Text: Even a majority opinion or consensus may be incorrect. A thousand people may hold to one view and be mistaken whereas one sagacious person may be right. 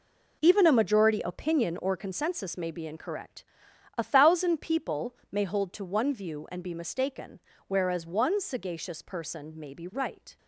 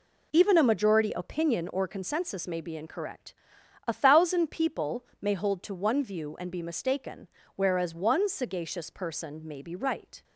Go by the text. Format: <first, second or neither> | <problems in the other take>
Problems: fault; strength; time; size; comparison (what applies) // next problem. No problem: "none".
second | gets quieter; strong; throughout; 10.5 dB // pauses between "people" and "may"; slight; at 5.1 s; 0.16 s long; slight in the second // pauses between "mistaken" and "whereas"; slight; at 7.3 s; 0.28 s long; slight in the second